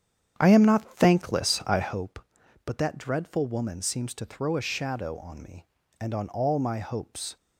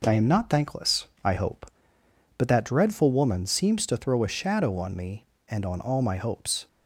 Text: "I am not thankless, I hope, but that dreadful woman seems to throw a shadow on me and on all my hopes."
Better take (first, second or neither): second